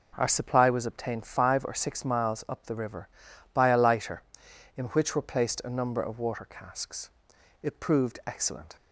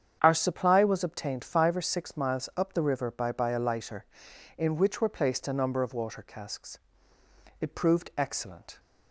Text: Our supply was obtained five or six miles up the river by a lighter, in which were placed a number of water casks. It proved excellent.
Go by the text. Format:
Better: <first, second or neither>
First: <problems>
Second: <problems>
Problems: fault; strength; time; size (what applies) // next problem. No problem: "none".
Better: first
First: none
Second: starts louder than the rest; strong; until 1.2 s; 8.5 dB // says "by" twice; at 3.3 s